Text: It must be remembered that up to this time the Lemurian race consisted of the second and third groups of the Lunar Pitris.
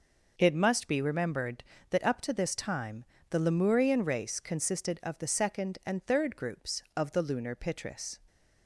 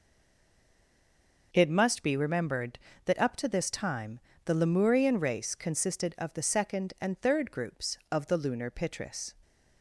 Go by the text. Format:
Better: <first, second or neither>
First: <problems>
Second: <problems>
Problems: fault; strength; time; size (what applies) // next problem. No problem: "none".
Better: first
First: pauses between "time" and "the"; slight; at 3.0 s; 0.24 s long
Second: stays silent before the first word; noticeable; until 1.5 s; 1.5 s long // pauses between "time" and "the"; slight; at 4.2 s; 0.24 s long